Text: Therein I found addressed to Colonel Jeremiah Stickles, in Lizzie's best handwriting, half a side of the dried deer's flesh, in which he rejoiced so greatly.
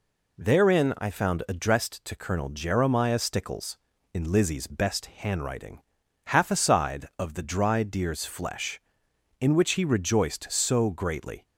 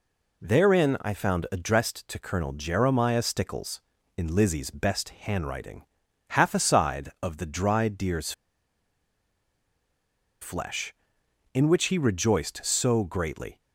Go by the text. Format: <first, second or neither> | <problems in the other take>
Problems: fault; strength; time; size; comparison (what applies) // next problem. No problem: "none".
first | pauses between "deer's" and "flesh"; strong; at 8.3 s; 2.0 s long